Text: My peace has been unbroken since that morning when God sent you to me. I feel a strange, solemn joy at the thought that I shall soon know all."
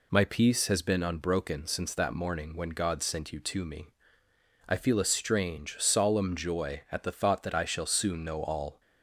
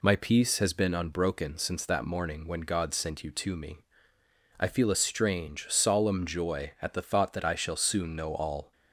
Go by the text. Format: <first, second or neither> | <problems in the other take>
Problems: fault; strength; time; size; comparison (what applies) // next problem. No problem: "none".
neither | none